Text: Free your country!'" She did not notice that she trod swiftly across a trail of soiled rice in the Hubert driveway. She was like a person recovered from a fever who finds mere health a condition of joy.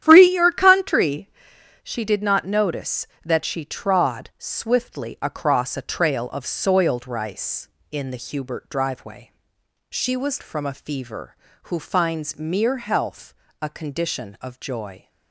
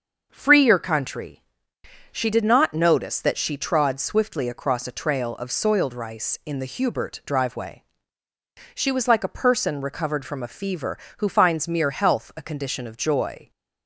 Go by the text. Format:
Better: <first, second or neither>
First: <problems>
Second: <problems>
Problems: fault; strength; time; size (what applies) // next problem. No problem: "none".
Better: second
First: starts louder than the rest; strong; until 1.0 s; 10.5 dB // skips "like a person recovered"; at 10.4 s // pauses between "health" and "a"; slight; at 13.3 s; 0.28 s long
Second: starts louder than the rest; until 1.3 s; 6.5 dB